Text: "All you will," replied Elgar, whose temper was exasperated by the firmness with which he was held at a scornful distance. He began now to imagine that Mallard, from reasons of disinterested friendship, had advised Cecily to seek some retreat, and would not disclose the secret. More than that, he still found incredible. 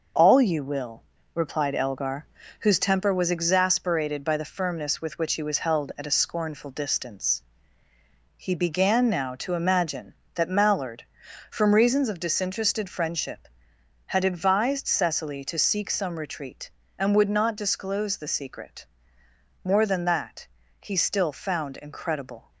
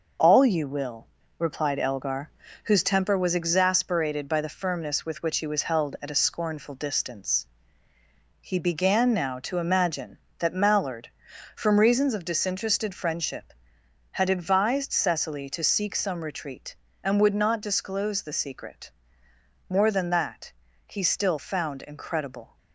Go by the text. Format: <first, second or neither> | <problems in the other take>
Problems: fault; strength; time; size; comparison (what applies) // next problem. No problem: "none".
neither | none